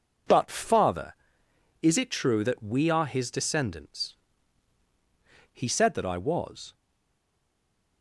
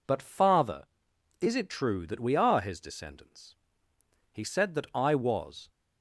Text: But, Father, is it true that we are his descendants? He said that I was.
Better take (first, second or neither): second